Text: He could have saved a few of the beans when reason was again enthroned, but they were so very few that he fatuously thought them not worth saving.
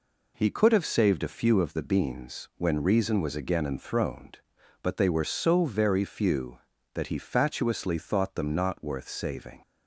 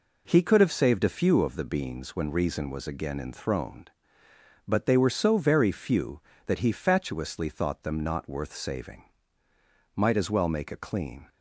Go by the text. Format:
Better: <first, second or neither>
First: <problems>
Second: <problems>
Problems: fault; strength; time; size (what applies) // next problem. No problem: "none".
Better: first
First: none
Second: goes on to say "Might as well make a clean"; from 9.9 s on; 1.3 s long